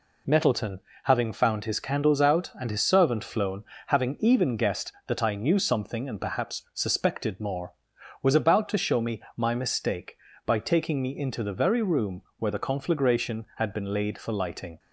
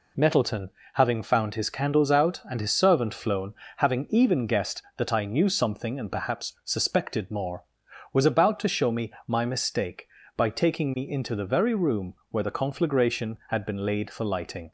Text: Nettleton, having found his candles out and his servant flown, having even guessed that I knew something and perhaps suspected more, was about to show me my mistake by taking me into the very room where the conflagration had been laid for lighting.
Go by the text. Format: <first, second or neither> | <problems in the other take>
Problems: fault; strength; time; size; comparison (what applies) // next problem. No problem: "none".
neither | pauses between "me" and "my"; slight; the same in both // pauses between "room" and "where"; slight; the same in both